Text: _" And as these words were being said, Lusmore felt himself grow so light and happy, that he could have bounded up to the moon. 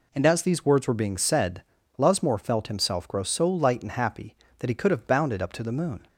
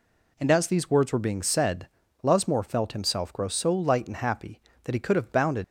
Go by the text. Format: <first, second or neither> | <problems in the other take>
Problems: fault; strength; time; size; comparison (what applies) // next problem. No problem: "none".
first | stops before "up to the moon"; at 5.6 s